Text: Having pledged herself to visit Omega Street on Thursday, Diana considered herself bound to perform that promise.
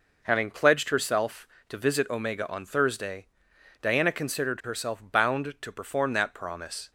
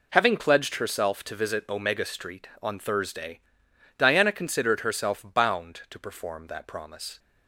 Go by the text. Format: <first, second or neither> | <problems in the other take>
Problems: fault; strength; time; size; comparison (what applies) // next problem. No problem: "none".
second | skips "Street"; at 2.4 s